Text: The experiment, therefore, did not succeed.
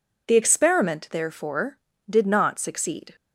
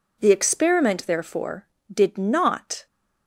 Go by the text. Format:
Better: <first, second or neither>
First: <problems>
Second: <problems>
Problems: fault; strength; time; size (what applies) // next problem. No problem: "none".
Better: first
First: none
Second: stops before "succeed"; at 2.8 s